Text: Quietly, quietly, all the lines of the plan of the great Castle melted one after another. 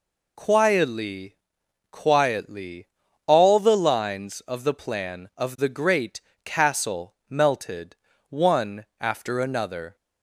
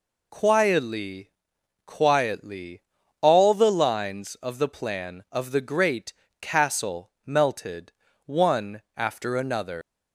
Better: first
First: pauses between "great" and "Castle"; slight; at 6.2 s; 0.22 s long // pauses between "Castle" and "melted"; slight; at 7.1 s; 0.16 s long // pauses between "melted" and "one"; slight; at 7.9 s; 0.34 s long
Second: pauses between "great" and "Castle"; slight; at 6.1 s; 0.26 s long // pauses between "Castle" and "melted"; slight; at 7.0 s; 0.16 s long // pauses between "melted" and "one"; slight; at 7.9 s; 0.34 s long // leaves "another" unfinished; at 9.8 s; 105 ms

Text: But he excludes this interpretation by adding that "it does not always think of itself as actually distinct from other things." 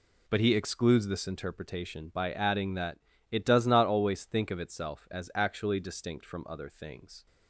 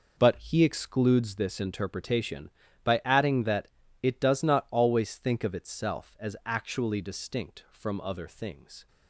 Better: neither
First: pauses between "that" and "it"; slight; at 2.9 s; 0.32 s long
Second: pauses between "that" and "it"; slight; at 3.6 s; 0.34 s long

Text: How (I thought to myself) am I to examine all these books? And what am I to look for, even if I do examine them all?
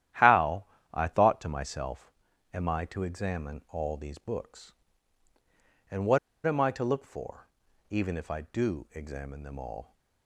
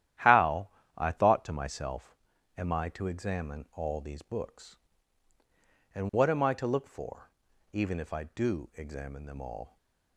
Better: second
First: starts louder than the rest; strong; until 1.4 s; 11.5 dB // pauses between "what" and "am"; slight; at 6.1 s; 0.26 s long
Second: starts louder than the rest; strong; until 1.4 s; 11.5 dB

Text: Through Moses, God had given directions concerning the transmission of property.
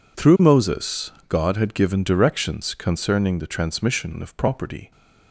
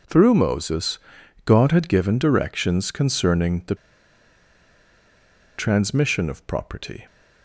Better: first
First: none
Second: pauses between "the" and "transmission"; strong; at 3.7 s; 1.8 s long

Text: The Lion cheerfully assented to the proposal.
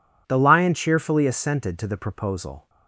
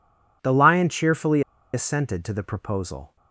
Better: first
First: none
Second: pauses between "cheerfully" and "assented"; slight; at 1.4 s; 0.32 s long

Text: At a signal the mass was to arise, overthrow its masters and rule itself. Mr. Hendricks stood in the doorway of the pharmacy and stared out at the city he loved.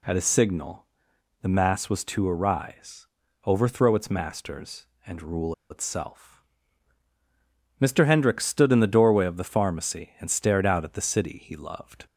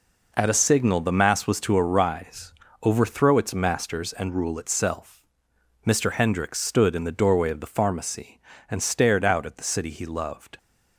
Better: second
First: pauses between "signal" and "the"; noticeable; at 0.8 s; 0.54 s long // pauses between "rule" and "itself"; slight; at 5.5 s; 0.16 s long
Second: none

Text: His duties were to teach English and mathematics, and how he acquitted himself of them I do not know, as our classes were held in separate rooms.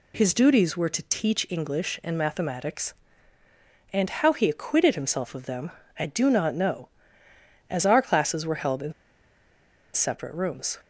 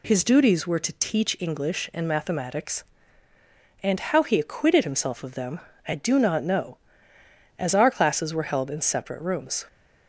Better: second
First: pauses between "them" and "I"; slight; at 5.7 s; 0.28 s long // pauses between "in" and "separate"; at 8.9 s; 1.0 s long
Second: pauses between "them" and "I"; slight; at 5.6 s; 0.28 s long

